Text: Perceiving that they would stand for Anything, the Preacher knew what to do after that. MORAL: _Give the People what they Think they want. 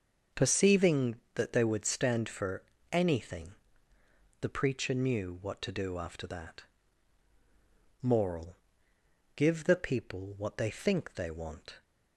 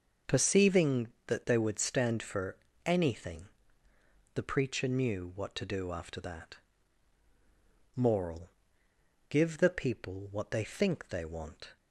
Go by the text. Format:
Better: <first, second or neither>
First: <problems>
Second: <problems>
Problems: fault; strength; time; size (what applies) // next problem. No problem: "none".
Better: neither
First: starts louder than the rest; noticeable; until 1.4 s; 6 dB // pauses between "for" and "Anything"; slight; at 2.6 s; 0.28 s long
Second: starts louder than the rest; noticeable; until 1.4 s; 6 dB // pauses between "for" and "Anything"; slight; at 2.5 s; 0.28 s long